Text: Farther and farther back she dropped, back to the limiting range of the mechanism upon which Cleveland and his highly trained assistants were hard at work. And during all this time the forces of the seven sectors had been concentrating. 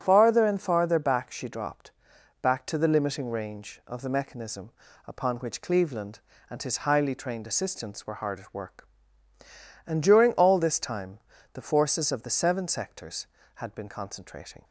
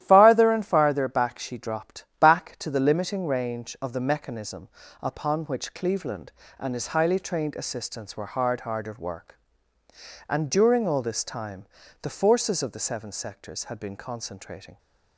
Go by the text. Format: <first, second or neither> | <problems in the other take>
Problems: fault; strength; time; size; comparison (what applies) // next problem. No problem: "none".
first | starts louder than the rest; strong; until 1.0 s; 12.5 dB; strong in the first // pauses between "mechanism" and "upon"; slight; at 4.6 s; 0.32 s long; slight in the first // says "hard" twice; at 8.6 s // pauses between "time" and "the"; slight; at 11.6 s; 0.36 s long; slight in the first